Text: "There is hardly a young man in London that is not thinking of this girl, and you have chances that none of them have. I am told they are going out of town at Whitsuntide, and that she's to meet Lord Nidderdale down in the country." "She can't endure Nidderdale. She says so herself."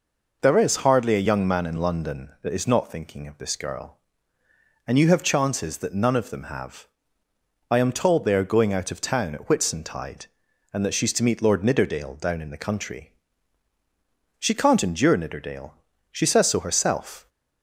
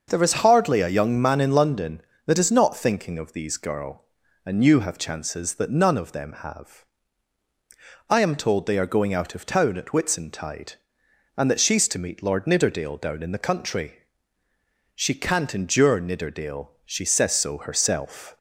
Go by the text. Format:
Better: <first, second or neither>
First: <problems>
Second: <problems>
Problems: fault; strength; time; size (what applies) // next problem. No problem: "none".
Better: first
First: none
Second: starts louder than the rest; until 1.0 s; 6.5 dB // says "these" for "this"; at 3.3 s